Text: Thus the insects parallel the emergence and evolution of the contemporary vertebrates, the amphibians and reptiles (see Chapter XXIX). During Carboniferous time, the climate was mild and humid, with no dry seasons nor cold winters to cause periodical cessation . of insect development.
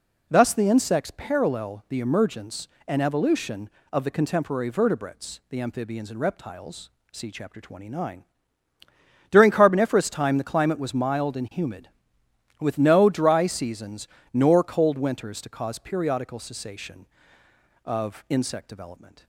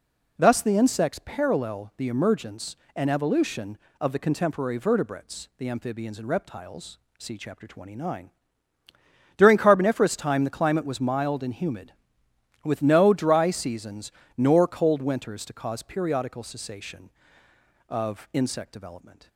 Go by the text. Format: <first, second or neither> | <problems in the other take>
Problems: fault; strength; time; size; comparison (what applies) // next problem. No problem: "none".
neither | pauses between "seasons" and "nor"; slight; the same in both